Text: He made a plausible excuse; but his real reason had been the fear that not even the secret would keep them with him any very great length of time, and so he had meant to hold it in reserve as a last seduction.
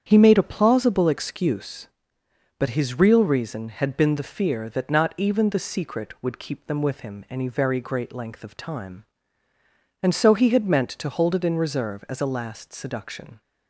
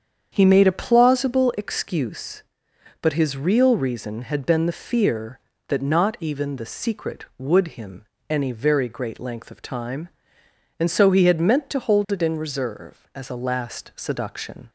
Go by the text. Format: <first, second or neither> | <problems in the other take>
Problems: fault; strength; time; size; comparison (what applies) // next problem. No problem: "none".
first | starts louder than the rest; strong; until 1.3 s; 7.5 dB; strong in the first // skips "keep them with"; at 7.7 s // pauses between "him" and "any"; slight; at 8.0 s; 0.26 s long